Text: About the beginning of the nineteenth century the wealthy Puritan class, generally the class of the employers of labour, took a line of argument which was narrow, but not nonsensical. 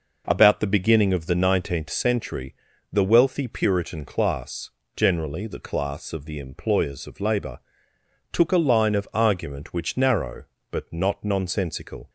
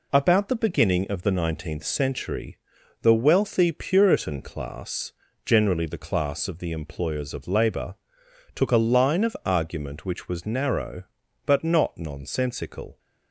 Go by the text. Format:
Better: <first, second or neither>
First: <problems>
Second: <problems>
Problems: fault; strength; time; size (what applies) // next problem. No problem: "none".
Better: second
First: pauses between "century" and "the"; slight; at 2.5 s; 0.36 s long // skips "was"; at 9.9 s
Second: pauses between "century" and "the"; noticeable; at 2.5 s; 0.46 s long